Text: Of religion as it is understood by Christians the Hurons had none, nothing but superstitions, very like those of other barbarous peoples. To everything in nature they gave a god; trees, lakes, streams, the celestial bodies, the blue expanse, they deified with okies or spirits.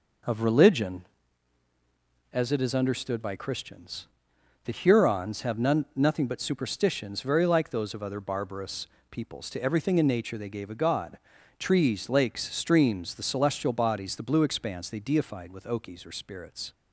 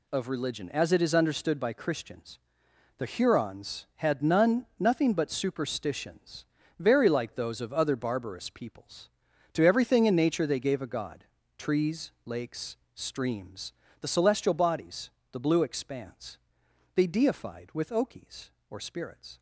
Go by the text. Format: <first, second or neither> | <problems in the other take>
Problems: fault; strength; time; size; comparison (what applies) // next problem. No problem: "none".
second | pauses between "Christians" and "the"; noticeable; at 4.0 s; 0.58 s long; noticeable in the second // says "have" for "had"; at 5.4 s // pauses between "barbarous" and "peoples"; slight; at 8.8 s; 0.24 s long